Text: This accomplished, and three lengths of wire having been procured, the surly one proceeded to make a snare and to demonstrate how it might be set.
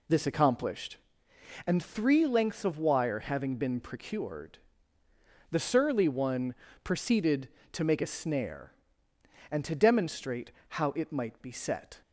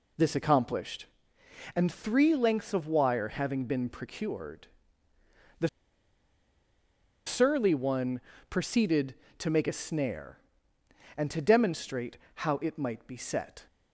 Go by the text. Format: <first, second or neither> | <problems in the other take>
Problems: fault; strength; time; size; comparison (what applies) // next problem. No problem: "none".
first | pauses between "the" and "surly"; strong; at 5.6 s; 1.5 s long // pauses between "one" and "proceeded"; slight; at 8.2 s; 0.28 s long; slight in the first // pauses between "demonstrate" and "how"; slight; at 12.1 s; 0.20 s long; slight in the first